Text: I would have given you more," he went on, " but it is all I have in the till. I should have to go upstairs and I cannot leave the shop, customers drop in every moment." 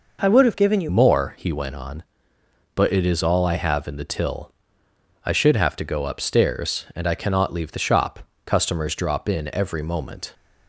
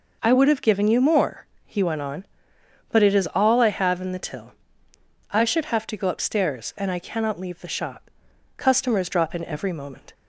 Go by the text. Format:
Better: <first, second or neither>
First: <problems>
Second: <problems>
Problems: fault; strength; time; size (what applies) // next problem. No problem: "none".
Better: second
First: changes voice at "more"; from 0.8 s on; 9.5 s long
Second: none